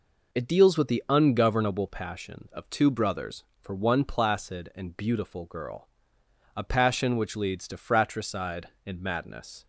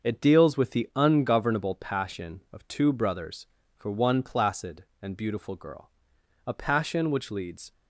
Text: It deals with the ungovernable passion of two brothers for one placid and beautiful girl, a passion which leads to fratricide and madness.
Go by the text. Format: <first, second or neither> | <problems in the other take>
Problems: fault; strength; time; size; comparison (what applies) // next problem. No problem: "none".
first | starts louder than the rest; until 1.1 s; 6 dB // stops before "to fratricide and madness"; at 7.7 s